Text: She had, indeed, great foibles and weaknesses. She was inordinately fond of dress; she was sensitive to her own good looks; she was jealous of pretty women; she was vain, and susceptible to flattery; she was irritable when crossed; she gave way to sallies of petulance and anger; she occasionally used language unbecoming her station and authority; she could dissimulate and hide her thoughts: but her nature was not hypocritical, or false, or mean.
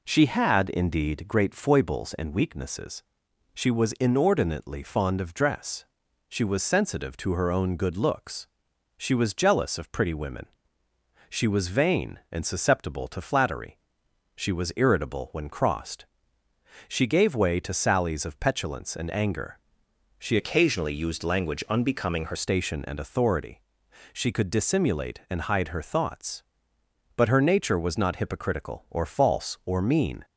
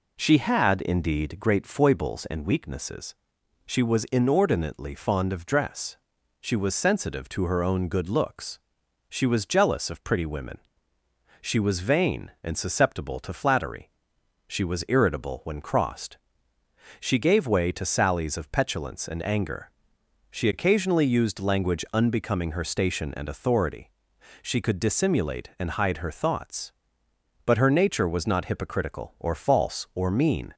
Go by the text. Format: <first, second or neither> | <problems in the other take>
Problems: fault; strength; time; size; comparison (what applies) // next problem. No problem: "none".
second | changes voice from "occasionally" to "her"; from 20.3 to 22.3 s; 2.0 s long